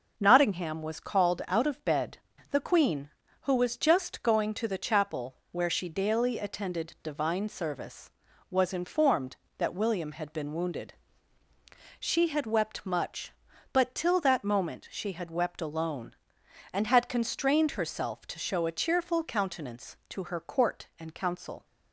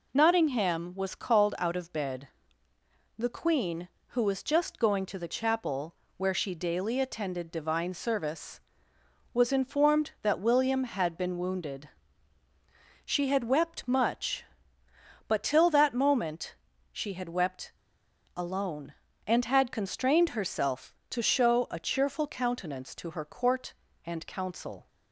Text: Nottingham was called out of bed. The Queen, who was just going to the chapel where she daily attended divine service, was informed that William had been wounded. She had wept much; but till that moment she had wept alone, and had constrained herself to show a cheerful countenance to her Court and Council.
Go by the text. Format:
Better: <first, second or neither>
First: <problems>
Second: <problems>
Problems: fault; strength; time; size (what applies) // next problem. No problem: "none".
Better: first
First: none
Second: pauses between "chapel" and "where"; slight; at 5.9 s; 0.22 s long // pauses between "moment" and "she"; slight; at 16.5 s; 0.36 s long // pauses between "wept" and "alone"; noticeable; at 17.7 s; 0.64 s long